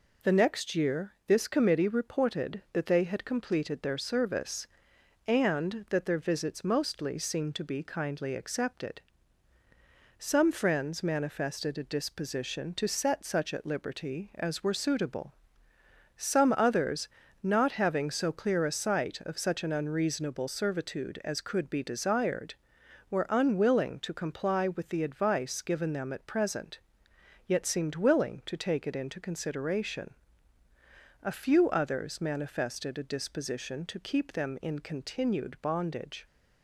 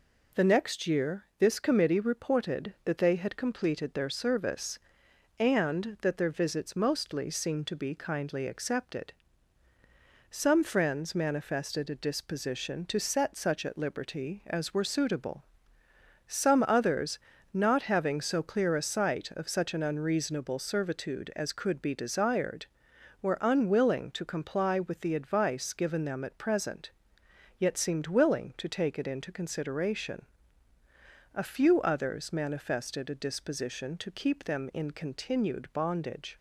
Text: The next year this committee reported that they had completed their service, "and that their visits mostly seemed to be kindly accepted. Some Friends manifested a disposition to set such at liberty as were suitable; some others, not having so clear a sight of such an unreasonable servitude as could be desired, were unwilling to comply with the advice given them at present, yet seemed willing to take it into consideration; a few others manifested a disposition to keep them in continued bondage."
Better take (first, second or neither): neither